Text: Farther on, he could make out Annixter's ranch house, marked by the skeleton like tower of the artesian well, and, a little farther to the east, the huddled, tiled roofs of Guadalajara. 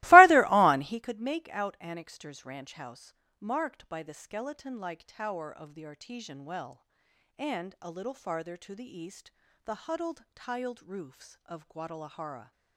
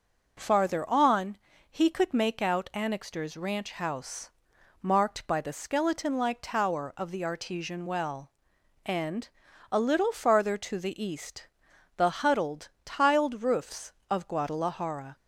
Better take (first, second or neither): second